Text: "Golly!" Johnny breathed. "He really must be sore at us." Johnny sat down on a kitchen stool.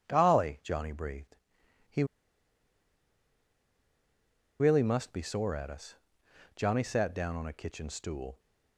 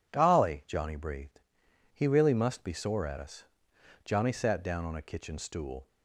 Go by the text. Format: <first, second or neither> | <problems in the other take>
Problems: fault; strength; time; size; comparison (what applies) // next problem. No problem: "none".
second | pauses between "He" and "really"; strong; at 2.0 s; 2.5 s long